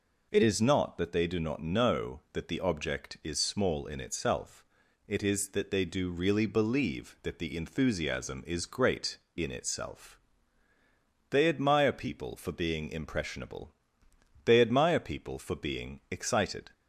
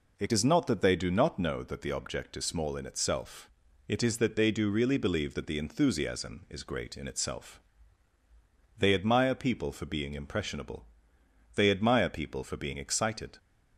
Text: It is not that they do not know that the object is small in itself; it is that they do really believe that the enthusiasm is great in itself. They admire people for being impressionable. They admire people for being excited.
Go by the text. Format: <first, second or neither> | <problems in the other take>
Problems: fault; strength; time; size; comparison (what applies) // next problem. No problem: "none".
neither | none